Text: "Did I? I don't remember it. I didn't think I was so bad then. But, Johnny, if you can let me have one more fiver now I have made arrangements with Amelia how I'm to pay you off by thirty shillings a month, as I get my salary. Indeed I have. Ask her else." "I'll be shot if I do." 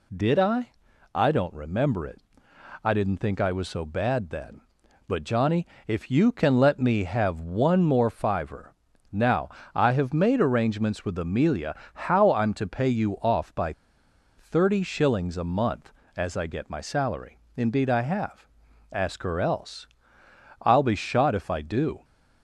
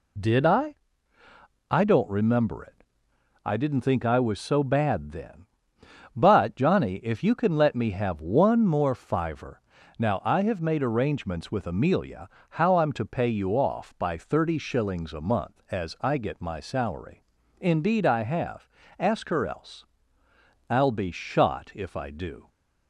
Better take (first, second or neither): second